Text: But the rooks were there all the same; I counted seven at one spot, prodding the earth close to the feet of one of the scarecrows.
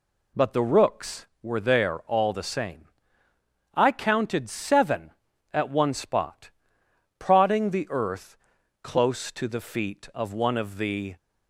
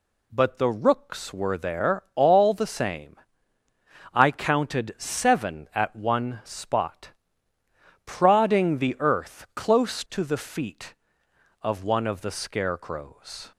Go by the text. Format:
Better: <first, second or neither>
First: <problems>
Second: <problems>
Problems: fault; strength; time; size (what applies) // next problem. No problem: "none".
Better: second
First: pauses between "earth" and "close"; noticeable; at 8.3 s; 0.48 s long // stops before "scarecrows"; at 11.1 s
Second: none